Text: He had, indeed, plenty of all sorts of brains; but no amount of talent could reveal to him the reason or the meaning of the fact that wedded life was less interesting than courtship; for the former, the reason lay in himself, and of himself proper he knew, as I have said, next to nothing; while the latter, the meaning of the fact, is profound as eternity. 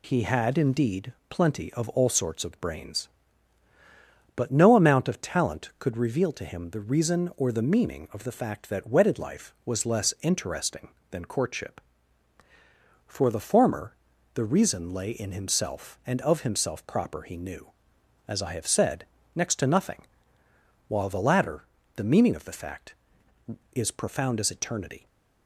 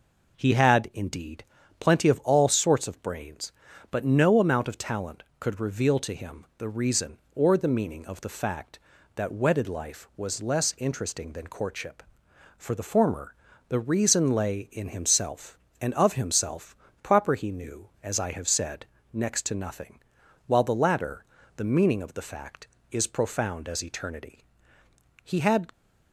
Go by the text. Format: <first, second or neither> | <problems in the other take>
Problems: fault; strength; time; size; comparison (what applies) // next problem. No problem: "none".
first | pauses between "himself" and "proper"; slight; at 16.7 s; 0.26 s long // goes on to say "He had"; from 25.2 s on; 0.48 s long